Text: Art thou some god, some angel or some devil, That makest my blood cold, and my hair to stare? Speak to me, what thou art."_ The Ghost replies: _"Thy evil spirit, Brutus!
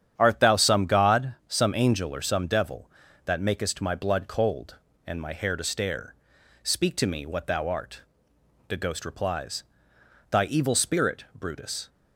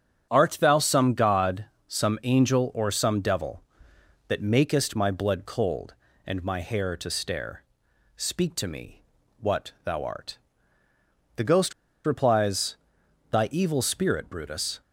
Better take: first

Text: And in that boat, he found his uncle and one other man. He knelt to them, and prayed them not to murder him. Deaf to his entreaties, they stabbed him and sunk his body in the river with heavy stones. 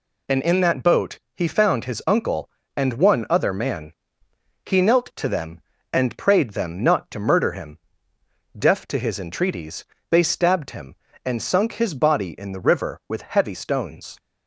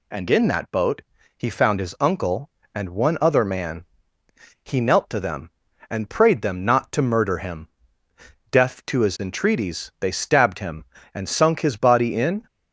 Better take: first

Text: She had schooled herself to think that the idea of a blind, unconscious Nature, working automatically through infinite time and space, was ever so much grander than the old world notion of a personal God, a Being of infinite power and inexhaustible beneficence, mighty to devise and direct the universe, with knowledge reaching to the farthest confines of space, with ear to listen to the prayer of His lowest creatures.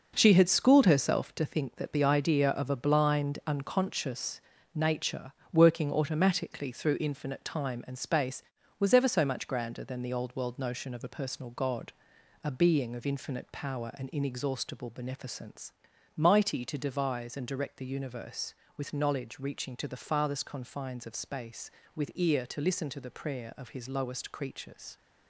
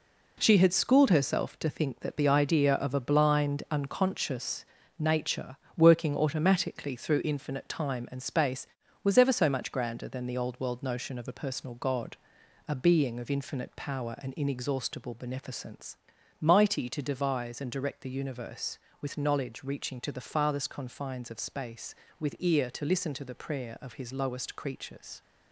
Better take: second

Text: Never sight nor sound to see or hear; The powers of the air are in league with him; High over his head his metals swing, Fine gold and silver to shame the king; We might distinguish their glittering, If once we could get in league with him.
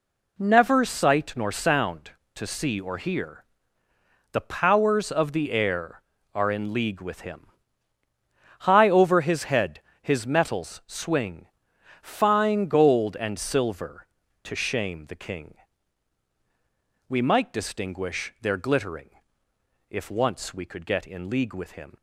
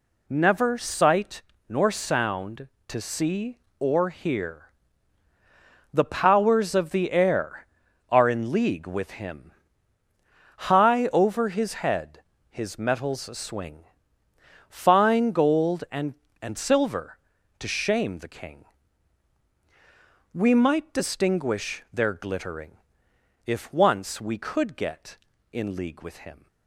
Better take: first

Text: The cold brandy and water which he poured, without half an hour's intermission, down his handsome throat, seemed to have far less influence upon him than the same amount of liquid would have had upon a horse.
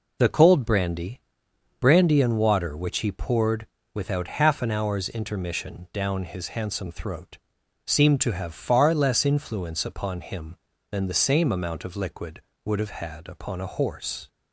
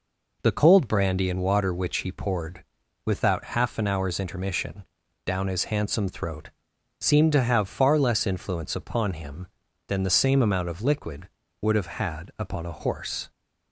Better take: second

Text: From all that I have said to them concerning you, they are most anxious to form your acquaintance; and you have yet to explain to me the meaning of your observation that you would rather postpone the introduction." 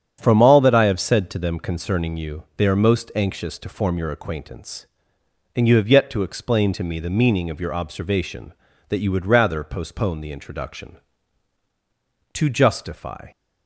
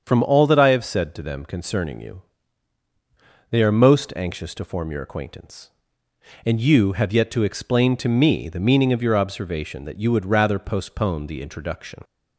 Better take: second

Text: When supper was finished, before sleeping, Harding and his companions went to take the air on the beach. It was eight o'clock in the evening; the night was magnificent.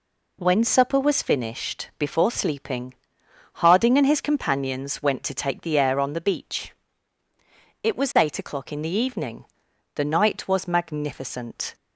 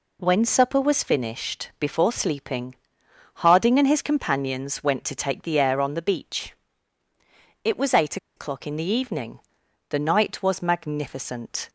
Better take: first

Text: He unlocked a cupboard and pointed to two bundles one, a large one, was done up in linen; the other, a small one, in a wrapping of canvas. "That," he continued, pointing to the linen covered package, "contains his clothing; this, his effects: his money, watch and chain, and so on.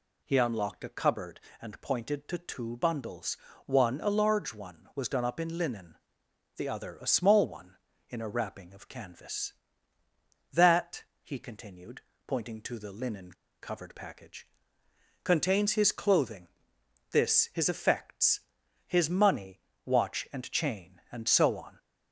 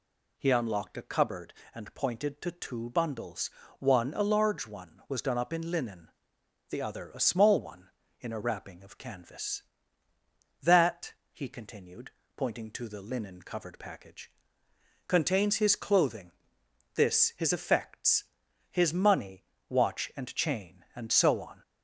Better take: second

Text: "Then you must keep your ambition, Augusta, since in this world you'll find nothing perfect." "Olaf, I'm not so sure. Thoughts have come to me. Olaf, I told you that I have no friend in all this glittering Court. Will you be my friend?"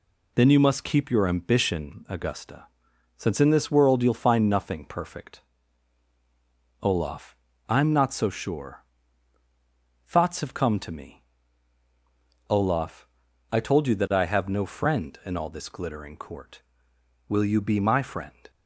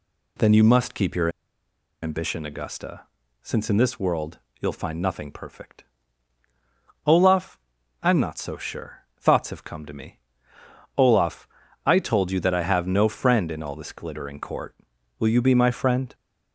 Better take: first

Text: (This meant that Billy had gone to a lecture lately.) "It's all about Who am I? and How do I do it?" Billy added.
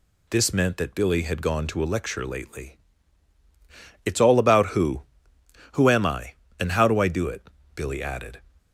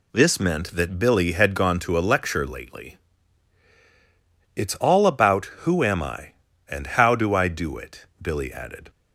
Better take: second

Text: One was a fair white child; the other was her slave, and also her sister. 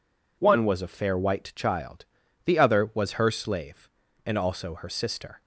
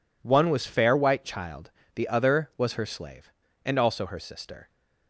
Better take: first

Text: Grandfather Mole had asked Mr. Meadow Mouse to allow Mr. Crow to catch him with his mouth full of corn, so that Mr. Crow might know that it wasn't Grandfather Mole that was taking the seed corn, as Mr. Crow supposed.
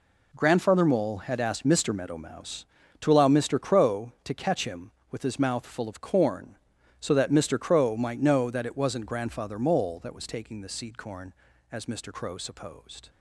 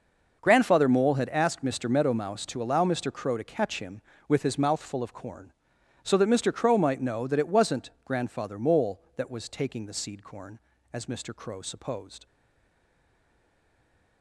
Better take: first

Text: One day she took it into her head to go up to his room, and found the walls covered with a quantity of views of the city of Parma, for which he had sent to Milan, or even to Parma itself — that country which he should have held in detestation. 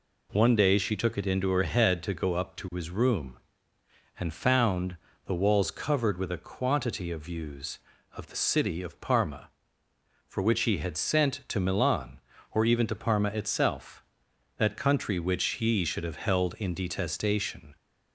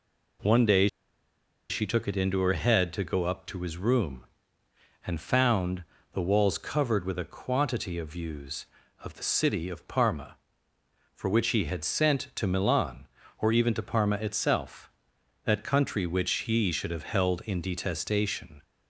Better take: first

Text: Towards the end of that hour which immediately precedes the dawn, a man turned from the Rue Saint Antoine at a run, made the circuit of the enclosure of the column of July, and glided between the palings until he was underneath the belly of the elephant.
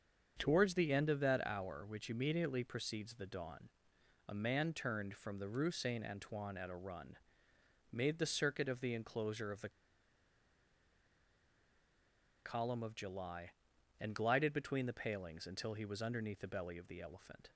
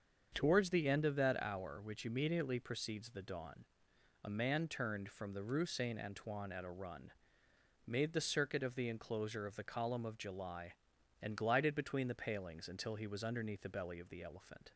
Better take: second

